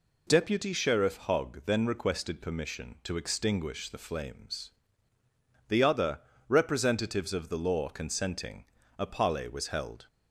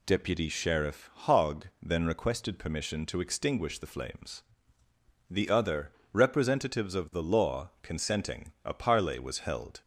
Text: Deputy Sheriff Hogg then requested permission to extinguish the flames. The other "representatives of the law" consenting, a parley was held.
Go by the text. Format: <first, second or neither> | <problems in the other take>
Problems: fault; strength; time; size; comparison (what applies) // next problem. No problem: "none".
neither | pauses between "other" and "representatives"; slight; the same in both